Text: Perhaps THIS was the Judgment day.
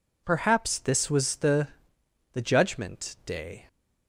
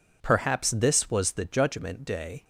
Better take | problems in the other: second | says "the" twice; at 2.3 s

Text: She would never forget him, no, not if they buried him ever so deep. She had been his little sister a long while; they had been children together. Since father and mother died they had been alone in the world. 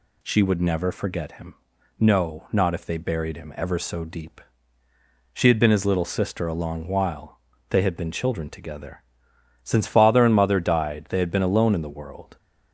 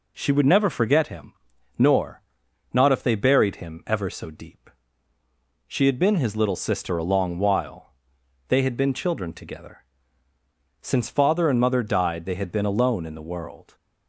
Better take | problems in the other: first | says "nor" for "no"; at 1.7 s

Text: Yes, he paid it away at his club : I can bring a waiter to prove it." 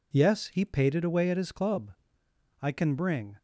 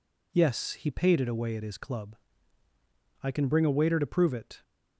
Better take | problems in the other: second | stops before "a waiter to prove it"; at 3.3 s

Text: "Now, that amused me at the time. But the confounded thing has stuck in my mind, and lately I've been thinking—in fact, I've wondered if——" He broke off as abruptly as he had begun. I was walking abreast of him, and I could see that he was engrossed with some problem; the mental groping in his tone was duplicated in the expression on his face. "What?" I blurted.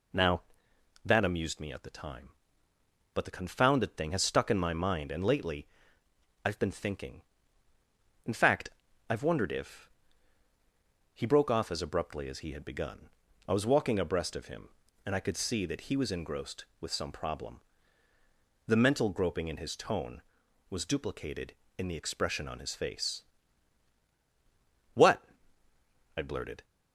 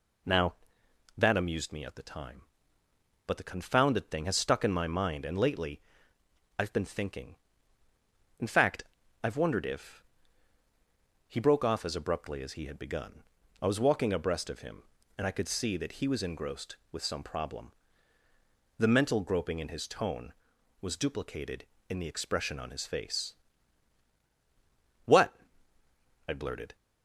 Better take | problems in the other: neither | pauses between "lately" and "I've"; noticeable; the same in both

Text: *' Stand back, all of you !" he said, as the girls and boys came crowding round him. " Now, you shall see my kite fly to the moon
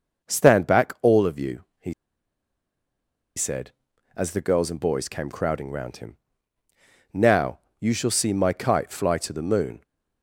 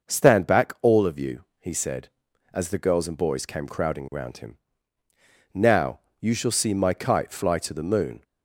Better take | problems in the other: second | starts louder than the rest; until 1.3 s; 6.5 dB; also in the second // pauses between "he" and "said"; strong; at 1.9 s; 1.4 s long

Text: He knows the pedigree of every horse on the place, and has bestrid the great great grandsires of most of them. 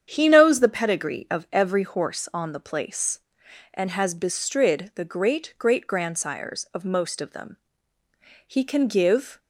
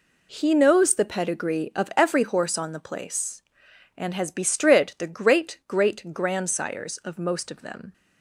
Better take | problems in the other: second | starts louder than the rest; strong; until 1.1 s; 8.5 dB // goes on to say "He can give"; noticeable; from 8.4 s on; 0.92 s long

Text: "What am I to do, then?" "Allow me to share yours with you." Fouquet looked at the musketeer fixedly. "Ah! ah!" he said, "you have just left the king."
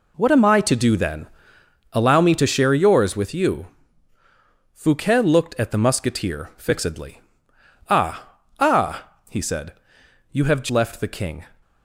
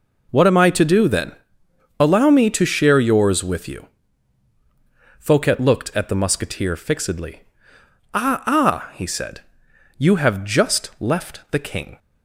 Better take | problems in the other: second | skips "just"; at 10.7 s

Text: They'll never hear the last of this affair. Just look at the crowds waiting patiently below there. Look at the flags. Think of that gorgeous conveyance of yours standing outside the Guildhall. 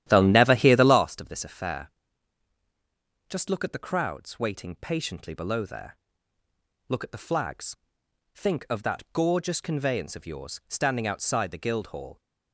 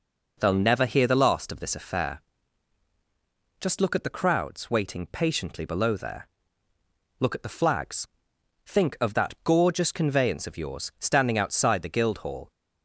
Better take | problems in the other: second | starts louder than the rest; strong; until 1.1 s; 12 dB

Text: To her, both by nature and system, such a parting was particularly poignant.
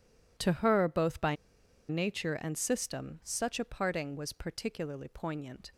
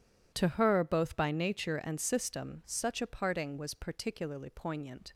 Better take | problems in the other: second | pauses between "by" and "nature"; noticeable; at 1.3 s; 0.53 s long

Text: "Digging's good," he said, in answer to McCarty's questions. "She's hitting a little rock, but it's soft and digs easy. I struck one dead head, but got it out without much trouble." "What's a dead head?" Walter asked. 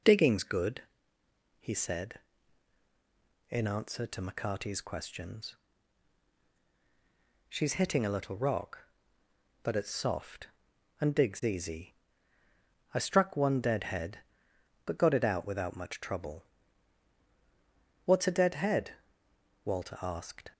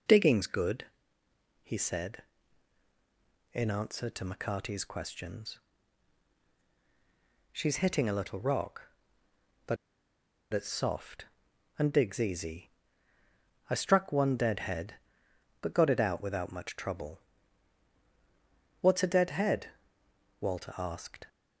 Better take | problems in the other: first | pauses between "but" and "it's"; noticeable; at 9.7 s; 0.77 s long

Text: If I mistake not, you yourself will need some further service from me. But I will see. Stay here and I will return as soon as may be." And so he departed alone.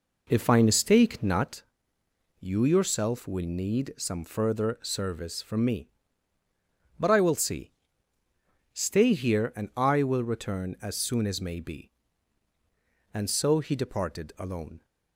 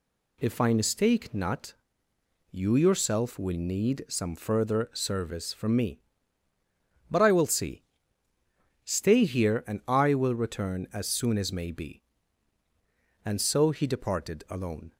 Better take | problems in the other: second | starts louder than the rest; noticeable; until 1.6 s; 4 dB

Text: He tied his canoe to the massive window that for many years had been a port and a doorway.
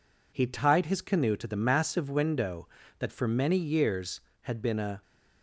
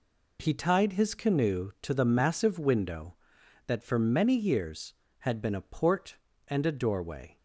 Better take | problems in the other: second | stops before "port and a doorway"; at 5.0 s

